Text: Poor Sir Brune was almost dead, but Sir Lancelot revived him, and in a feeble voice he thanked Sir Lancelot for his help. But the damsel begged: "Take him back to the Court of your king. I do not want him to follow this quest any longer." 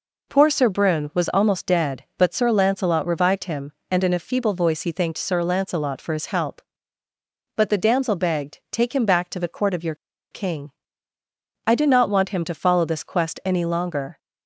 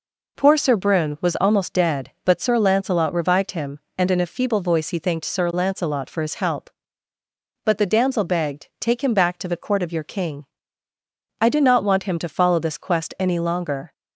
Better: second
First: pauses between "your" and "king"; at 9.9 s; 0.37 s long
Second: none

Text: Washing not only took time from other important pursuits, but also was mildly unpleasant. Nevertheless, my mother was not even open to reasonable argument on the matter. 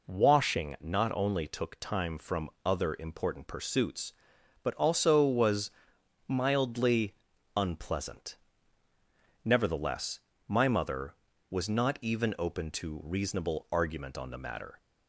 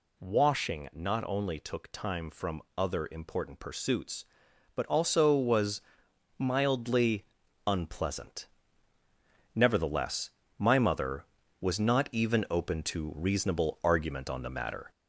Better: first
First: pauses between "from" and "other"; slight; at 2.4 s; 0.16 s long // pauses between "was" and "mildly"; noticeable; at 5.6 s; 0.58 s long // pauses between "mildly" and "unpleasant"; at 7.1 s; 0.42 s long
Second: gets louder; slight; throughout; 2.5 dB // pauses between "from" and "other"; slight; at 2.6 s; 0.16 s long // pauses between "was" and "mildly"; noticeable; at 5.8 s; 0.58 s long // pauses between "mildly" and "unpleasant"; at 7.2 s; 0.42 s long

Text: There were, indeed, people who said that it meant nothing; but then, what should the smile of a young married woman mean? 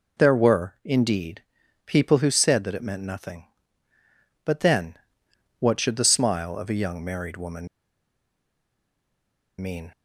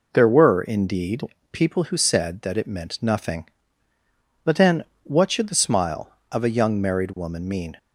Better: second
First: pauses between "woman" and "mean"; strong; at 7.6 s; 1.9 s long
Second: none

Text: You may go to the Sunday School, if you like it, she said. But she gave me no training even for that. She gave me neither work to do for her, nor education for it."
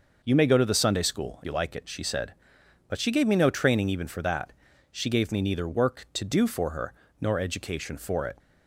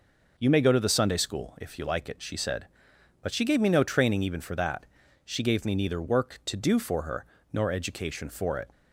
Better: second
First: skips "if"; at 1.4 s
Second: none

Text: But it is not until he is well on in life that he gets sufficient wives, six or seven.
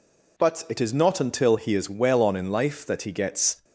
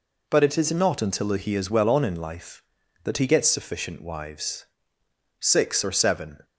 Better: second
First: stops before "sufficient wives six or seven"; at 3.6 s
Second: none

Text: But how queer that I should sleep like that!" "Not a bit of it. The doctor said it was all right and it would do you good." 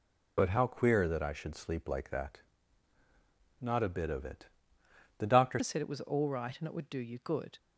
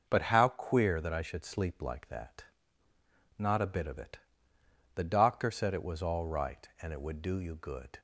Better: second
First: changes voice at "said"; from 5.6 s on; 1.9 s long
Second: none

